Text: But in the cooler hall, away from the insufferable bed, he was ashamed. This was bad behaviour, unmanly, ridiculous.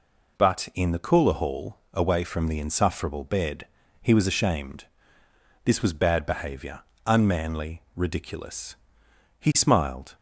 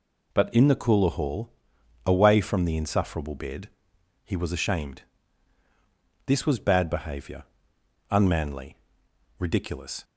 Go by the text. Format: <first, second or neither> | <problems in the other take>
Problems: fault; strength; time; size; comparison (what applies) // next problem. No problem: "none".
second | goes on to say "He smiled"; noticeable; from 9.3 s on; 0.74 s long